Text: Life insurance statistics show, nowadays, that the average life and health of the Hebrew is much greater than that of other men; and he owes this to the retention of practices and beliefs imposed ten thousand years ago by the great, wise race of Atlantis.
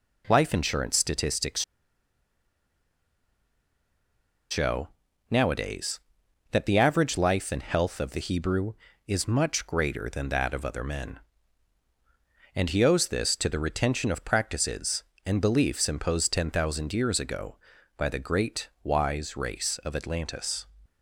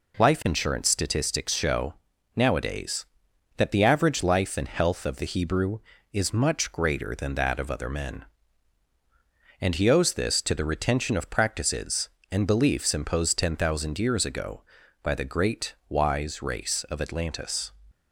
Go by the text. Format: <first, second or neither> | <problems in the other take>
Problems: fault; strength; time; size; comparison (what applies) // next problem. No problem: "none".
second | pauses between "statistics" and "show"; strong; at 1.6 s; 2.8 s long